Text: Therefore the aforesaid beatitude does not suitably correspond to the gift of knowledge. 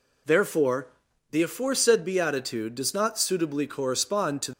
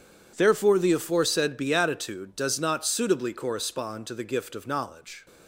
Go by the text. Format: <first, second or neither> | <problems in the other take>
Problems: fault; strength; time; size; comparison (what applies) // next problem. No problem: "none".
second | pauses between "Therefore" and "the"; at 0.8 s; 0.44 s long // stops before "the gift of knowledge"; at 4.5 s